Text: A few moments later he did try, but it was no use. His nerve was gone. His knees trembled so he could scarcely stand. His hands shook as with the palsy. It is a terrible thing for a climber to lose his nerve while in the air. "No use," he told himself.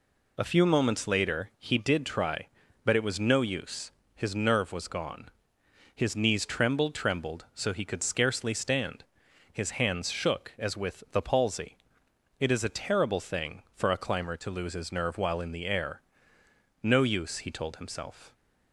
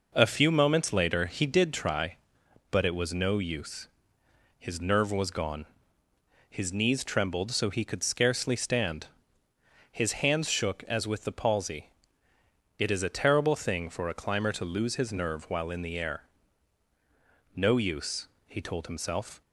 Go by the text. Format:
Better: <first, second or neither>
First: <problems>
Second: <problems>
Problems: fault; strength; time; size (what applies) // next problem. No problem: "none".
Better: second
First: says "trembled" twice; at 6.9 s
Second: none